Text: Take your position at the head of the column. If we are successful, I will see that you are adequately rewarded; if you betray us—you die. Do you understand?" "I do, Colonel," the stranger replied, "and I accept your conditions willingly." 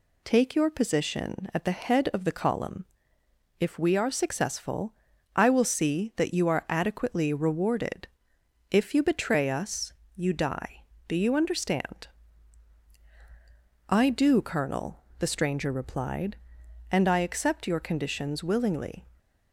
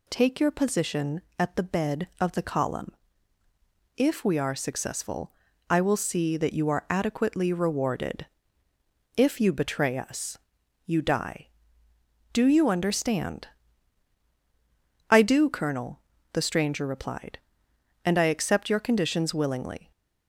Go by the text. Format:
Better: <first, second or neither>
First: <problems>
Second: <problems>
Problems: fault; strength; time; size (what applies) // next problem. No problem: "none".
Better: first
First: none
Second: says "bed" for "head"; at 1.6 s